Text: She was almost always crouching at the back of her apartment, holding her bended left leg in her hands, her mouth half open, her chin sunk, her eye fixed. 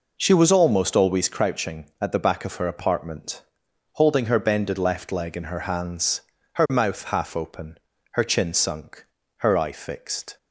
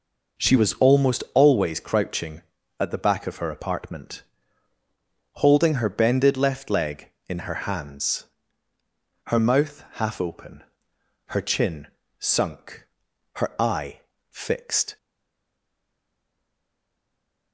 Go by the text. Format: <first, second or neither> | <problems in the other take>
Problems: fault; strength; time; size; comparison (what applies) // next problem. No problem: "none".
first | pauses between "chin" and "sunk"; slight; at 11.8 s; 0.32 s long // pauses between "eye" and "fixed"; slight; at 14.0 s; 0.28 s long // stays silent after the last word; strong; from 14.9 s on; 2.6 s long